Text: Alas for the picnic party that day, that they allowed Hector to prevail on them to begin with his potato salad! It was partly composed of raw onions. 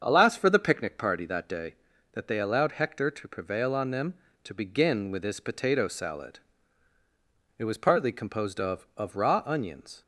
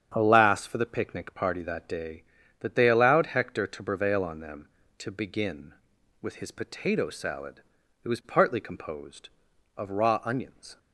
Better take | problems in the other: second | starts louder than the rest; strong; until 1.0 s; 7 dB; strong in the second // says "of" twice; at 8.9 s

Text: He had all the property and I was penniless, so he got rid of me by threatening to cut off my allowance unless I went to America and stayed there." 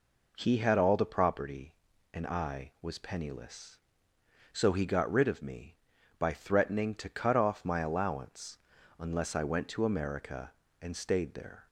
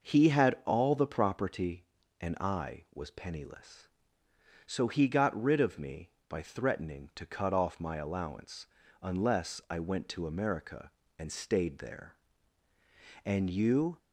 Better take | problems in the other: first | pauses between "allowance" and "unless"; slight; at 8.6 s; 0.34 s long; also in the first // goes on to say "And you"; noticeable; from 13.2 s on; 0.74 s long

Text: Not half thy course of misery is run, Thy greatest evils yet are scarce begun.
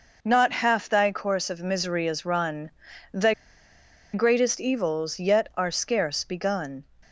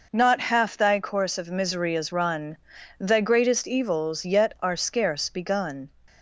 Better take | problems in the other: second | pauses between "Thy" and "greatest"; noticeable; at 3.3 s; 0.81 s long

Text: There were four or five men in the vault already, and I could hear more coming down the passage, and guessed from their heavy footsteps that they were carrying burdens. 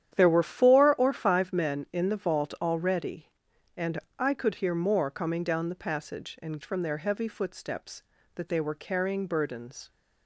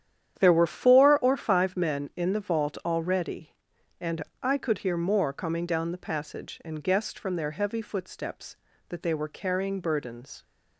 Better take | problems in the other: second | starts louder than the rest; strong; until 1.1 s; 10 dB; strong in the second // pauses between "and" and "I"; slight; at 3.9 s; 0.22 s long; slight in the second // skips "guessed"; at 6.6 s

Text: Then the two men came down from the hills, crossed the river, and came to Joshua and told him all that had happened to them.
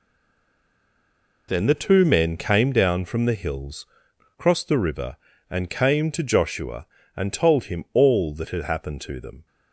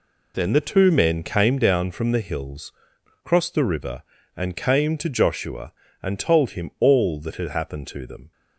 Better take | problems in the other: second | stays silent before the first word; noticeable; until 1.4 s; 1.4 s long

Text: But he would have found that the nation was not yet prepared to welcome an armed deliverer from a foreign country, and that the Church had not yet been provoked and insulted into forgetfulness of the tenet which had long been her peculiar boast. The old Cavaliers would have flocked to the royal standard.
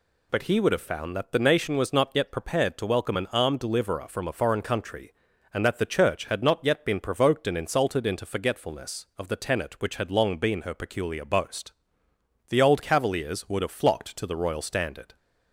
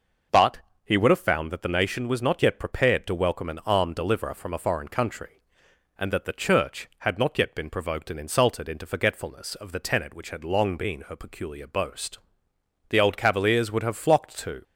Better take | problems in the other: first | pauses between "But" and "he"; slight; at 0.5 s; 0.26 s long // stops before "the royal standard"; at 14.6 s

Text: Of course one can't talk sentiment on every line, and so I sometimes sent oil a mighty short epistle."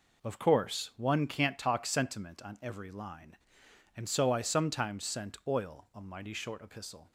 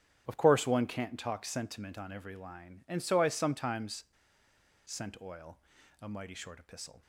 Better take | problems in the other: first | starts louder than the rest; strong; until 1.2 s; 10 dB // pauses between "sometimes" and "sent"; noticeable; at 4.0 s; 0.82 s long // pauses between "oil" and "a"; at 5.5 s; 0.44 s long

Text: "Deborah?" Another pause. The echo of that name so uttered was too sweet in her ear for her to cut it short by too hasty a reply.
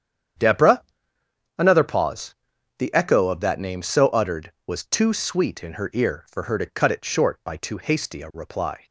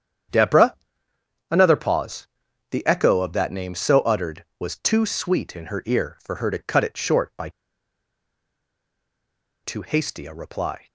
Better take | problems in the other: first | starts louder than the rest; strong; until 2.0 s; 9 dB; strong in the first // pauses between "by" and "too"; strong; at 7.4 s; 2.1 s long

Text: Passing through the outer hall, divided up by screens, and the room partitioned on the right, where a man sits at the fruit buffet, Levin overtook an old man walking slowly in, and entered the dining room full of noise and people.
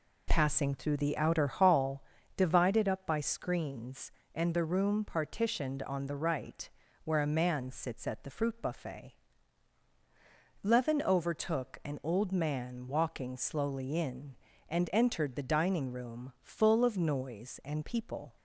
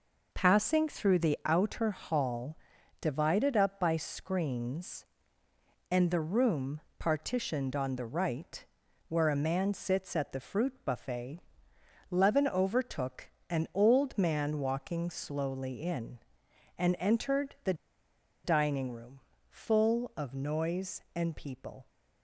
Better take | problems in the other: first | pauses between "room" and "partitioned"; slight; at 6.7 s; 0.18 s long // pauses between "overtook" and "an"; slight; at 13.2 s; 0.20 s long // pauses between "the" and "dining"; noticeable; at 17.7 s; 0.70 s long // pauses between "room" and "full"; slight; at 19.2 s; 0.28 s long

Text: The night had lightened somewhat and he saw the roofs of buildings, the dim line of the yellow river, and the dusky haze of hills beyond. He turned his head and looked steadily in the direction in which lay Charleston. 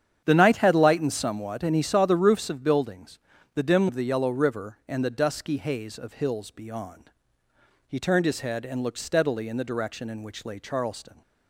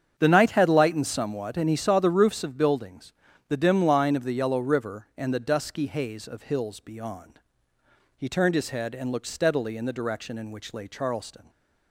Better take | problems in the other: second | starts louder than the rest; strong; until 1.2 s; 9 dB; strong in the second // skips "line"; at 3.8 s

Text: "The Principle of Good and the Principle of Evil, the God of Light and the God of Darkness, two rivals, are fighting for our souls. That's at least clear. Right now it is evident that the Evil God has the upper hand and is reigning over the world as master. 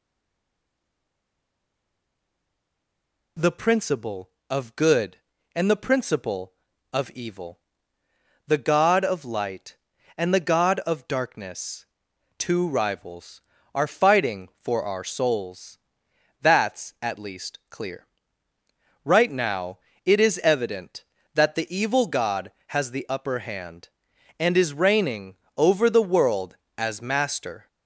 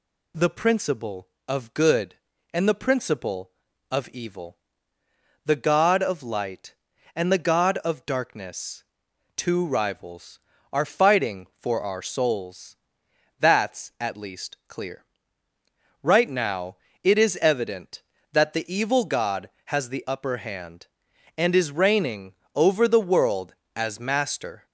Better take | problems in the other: second | stays silent before the first word; strong; until 3.3 s; 3.3 s long // pauses between "now" and "it"; slight; at 19.7 s; 0.26 s long; slight in the second // pauses between "reigning" and "over"; slight; at 25.3 s; 0.20 s long; slight in the second

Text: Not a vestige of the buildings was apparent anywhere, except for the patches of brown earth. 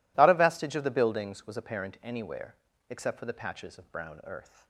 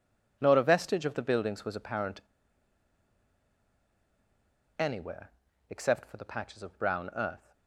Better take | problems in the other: first | pauses between "apparent" and "anywhere"; strong; at 2.2 s; 2.5 s long

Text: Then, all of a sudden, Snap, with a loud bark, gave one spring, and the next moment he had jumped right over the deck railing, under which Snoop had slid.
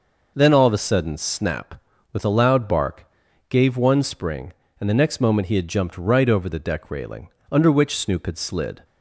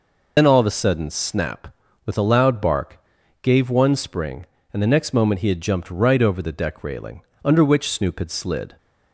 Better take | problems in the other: first | loses the start of "Then"; at 0.3 s; 80 ms

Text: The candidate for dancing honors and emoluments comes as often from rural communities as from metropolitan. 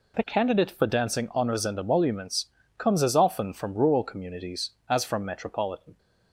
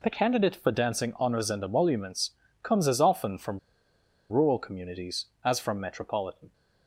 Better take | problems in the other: first | pauses between "emoluments" and "comes"; slight; at 2.3 s; 0.34 s long; slight in the first // pauses between "from" and "rural"; noticeable; at 3.5 s; 0.71 s long

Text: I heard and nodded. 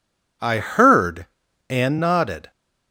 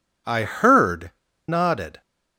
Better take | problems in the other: first | skips "and"; at 1.2 s

